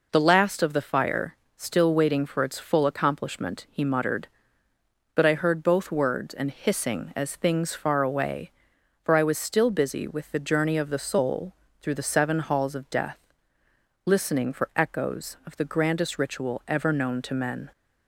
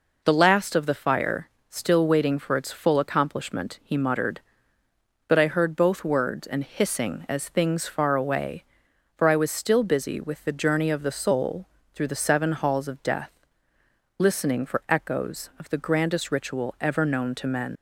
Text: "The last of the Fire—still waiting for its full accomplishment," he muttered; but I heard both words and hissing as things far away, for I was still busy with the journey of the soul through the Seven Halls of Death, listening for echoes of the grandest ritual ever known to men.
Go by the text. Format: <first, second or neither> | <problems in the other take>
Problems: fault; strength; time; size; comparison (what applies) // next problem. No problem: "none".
first | pauses between "soul" and "through"; slight; at 11.6 s; 0.26 s long; slight in the first // leaves "men" unfinished; at 17.7 s; 90 ms